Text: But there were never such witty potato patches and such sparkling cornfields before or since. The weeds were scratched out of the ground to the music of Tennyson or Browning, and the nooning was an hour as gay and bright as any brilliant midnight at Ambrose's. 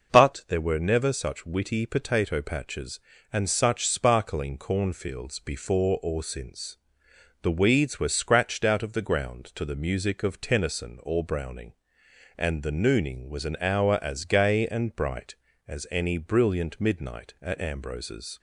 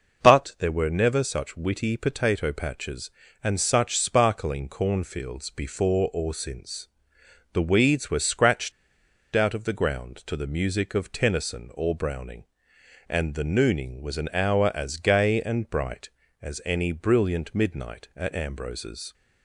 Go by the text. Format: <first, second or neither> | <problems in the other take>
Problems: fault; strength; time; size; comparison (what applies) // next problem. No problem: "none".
first | pauses between "scratched" and "out"; noticeable; at 8.7 s; 0.63 s long